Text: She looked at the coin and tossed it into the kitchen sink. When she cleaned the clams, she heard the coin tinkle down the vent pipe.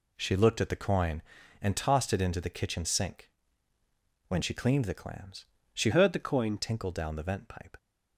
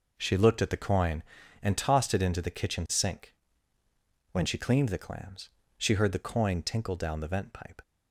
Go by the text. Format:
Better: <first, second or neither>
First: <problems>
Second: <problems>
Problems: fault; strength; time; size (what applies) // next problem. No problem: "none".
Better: second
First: changes voice from "heard" to "coin"; from 5.9 to 6.5 s; 0.6 s long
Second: none